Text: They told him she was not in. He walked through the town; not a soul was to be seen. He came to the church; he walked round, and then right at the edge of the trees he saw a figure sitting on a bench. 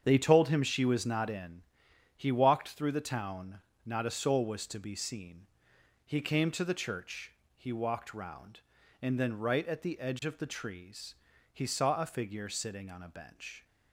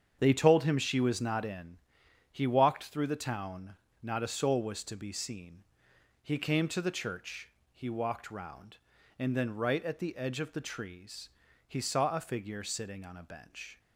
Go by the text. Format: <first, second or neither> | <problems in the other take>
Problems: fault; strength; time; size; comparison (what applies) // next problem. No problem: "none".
neither | starts louder than the rest; strong; the same in both // pauses between "trees" and "he"; the same in both